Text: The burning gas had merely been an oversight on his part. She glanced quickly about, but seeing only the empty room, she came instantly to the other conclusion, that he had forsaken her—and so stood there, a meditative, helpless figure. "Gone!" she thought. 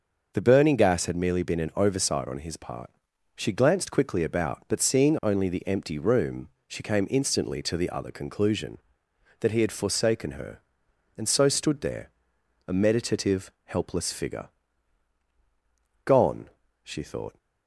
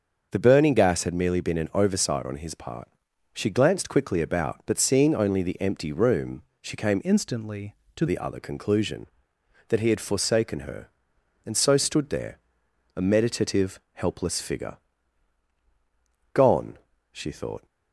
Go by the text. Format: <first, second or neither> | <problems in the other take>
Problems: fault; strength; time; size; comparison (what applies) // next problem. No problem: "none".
first | starts louder than the rest; until 1.3 s; 6.5 dB; also in the first // changes voice from "instantly" to "to"; from 7.0 to 8.0 s; 1.0 s long